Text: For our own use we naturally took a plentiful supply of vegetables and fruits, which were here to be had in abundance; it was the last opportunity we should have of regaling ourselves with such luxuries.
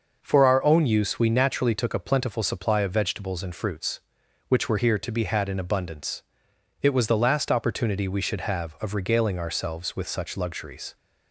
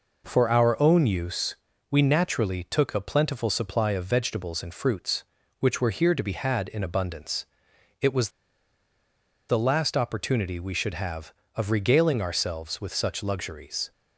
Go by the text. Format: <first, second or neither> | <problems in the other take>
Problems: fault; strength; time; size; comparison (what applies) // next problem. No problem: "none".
first | pauses between "use" and "we"; slight; at 1.5 s; 0.36 s long // pauses between "was" and "the"; at 8.2 s; 1.1 s long